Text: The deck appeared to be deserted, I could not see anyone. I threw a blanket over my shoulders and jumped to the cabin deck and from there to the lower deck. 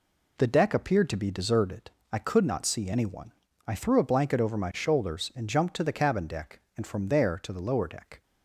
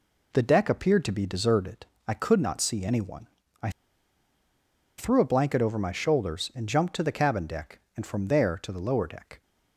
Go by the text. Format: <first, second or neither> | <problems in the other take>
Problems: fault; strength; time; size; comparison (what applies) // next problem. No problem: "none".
first | pauses between "I" and "threw"; strong; at 3.6 s; 1.2 s long